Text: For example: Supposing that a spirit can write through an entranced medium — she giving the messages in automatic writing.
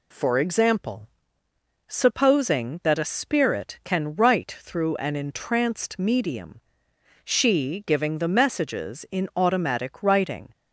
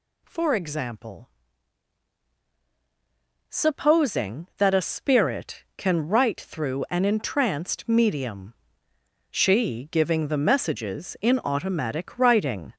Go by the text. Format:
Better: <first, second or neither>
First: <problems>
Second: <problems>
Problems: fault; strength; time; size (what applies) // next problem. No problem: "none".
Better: first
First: none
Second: gets louder; noticeable; throughout; 5.5 dB